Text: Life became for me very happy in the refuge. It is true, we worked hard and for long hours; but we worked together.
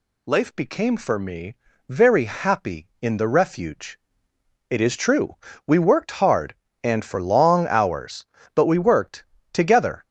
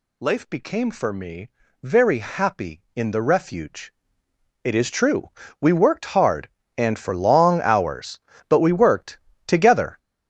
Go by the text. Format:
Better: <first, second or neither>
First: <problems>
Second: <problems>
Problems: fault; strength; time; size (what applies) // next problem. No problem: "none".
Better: first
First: pauses between "me" and "very"; slight; at 1.5 s; 0.32 s long // pauses between "worked" and "together"; slight; at 9.2 s; 0.28 s long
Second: gets louder; strong; throughout; 9.5 dB // pauses between "me" and "very"; slight; at 1.4 s; 0.32 s long // pauses between "worked" and "together"; slight; at 9.1 s; 0.28 s long